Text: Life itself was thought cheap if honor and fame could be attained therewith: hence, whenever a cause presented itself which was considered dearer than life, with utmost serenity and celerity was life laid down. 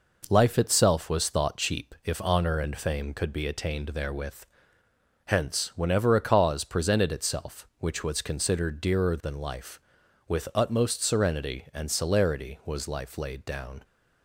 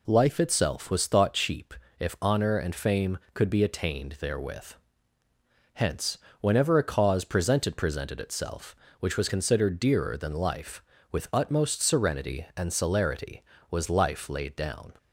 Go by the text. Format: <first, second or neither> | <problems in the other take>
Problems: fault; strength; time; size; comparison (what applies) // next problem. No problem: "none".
first | pauses between "cheap" and "if"; slight; at 1.7 s; 0.24 s long // says "presented" twice; at 7.7 s